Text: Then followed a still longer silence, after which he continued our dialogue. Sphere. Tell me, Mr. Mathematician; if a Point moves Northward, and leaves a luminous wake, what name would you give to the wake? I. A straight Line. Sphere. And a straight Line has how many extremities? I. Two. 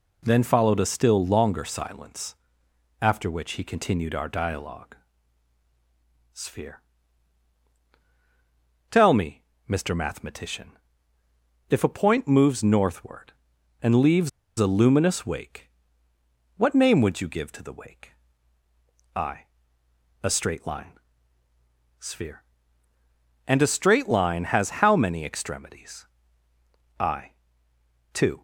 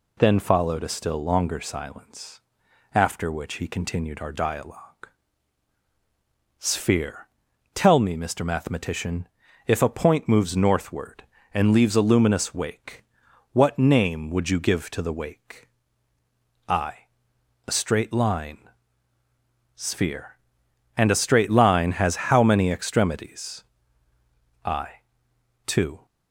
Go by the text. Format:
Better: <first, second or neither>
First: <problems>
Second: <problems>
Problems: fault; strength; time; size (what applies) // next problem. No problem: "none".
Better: second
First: pauses between "leaves" and "a"; slight; at 14.2 s; 0.28 s long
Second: none